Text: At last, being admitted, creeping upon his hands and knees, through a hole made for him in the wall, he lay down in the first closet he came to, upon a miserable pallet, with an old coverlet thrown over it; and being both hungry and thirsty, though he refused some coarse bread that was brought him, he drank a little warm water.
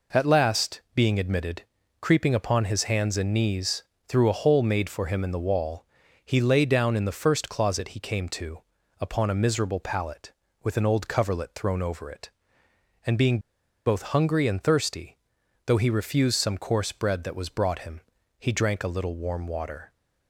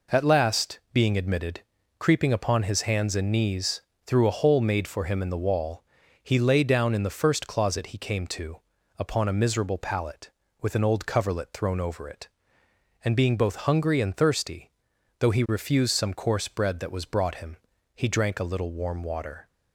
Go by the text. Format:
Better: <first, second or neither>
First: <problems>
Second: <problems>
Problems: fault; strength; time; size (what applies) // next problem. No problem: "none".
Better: second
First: pauses between "being" and "both"; noticeable; at 13.3 s; 0.46 s long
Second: none